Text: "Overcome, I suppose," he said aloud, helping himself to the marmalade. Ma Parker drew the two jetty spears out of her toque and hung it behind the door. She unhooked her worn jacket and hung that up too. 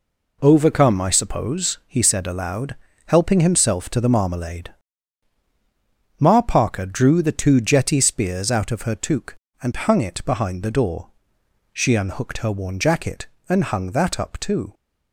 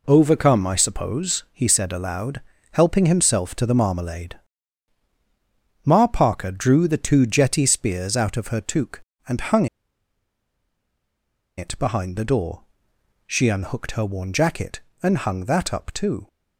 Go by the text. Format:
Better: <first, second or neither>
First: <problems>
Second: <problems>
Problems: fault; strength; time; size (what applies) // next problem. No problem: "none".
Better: first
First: none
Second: pauses between "hung" and "it"; strong; at 9.6 s; 1.9 s long